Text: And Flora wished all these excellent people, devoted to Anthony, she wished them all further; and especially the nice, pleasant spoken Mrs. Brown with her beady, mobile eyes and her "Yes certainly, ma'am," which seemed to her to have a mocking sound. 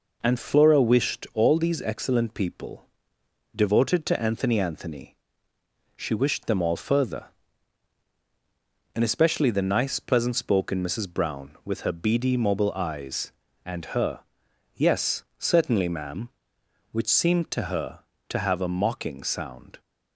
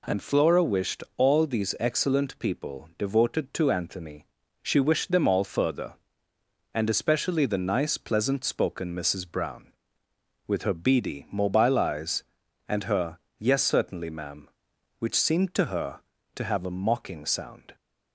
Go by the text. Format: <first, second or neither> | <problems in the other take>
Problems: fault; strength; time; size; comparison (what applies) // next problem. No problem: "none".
second | says "Anthony" twice; at 4.5 s // pauses between "her" and "Yes"; noticeable; at 14.2 s; 0.54 s long; slight in the second // pauses between "Yes" and "certainly"; slight; at 15.2 s; 0.16 s long